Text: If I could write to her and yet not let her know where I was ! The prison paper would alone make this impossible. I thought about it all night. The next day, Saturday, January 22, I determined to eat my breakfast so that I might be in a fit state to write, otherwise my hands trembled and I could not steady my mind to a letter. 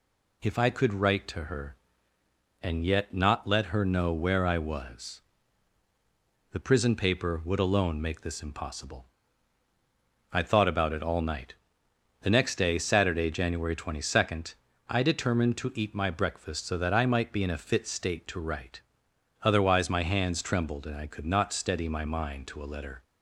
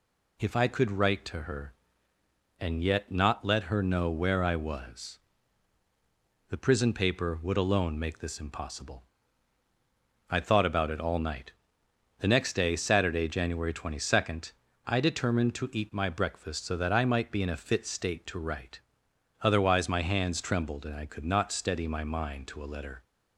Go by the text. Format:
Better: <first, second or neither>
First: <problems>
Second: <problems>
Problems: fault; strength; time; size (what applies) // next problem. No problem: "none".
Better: neither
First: none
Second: none